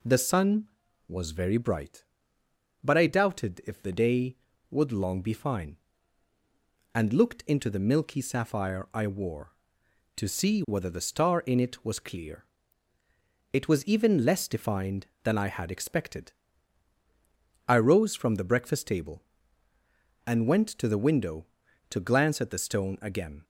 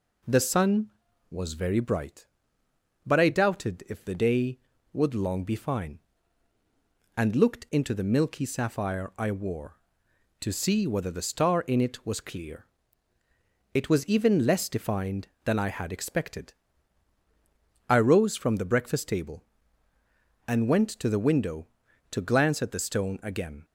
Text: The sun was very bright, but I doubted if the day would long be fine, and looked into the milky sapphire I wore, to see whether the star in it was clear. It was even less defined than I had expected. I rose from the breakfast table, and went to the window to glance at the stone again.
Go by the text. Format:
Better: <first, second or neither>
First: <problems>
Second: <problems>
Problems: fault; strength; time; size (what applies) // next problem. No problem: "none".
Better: neither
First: none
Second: none